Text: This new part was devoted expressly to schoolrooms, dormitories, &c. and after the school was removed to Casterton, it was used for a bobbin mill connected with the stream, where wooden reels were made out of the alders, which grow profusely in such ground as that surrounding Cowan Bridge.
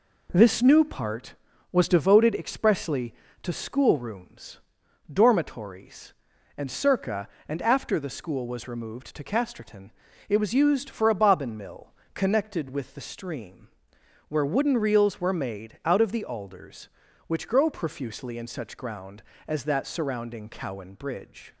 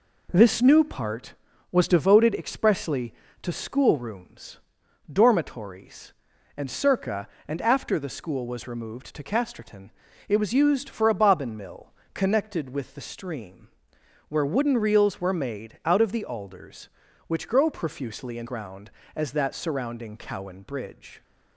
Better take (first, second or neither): first